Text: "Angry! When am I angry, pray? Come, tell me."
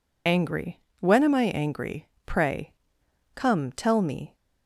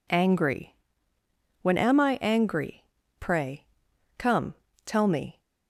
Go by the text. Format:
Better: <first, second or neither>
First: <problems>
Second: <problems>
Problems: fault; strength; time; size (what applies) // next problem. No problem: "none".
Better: second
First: loses the start of "Angry"; at 0.2 s; 45 ms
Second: none